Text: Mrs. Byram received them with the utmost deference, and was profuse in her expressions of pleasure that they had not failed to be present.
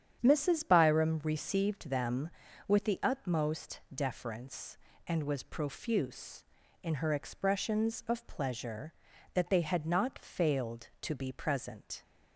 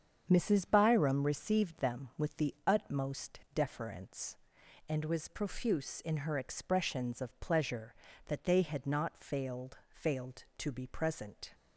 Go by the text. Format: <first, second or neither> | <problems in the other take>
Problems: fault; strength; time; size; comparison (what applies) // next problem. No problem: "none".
first | starts louder than the rest; strong; until 1.3 s; 7.5 dB; strong in the first // says "failed" twice; at 9.9 s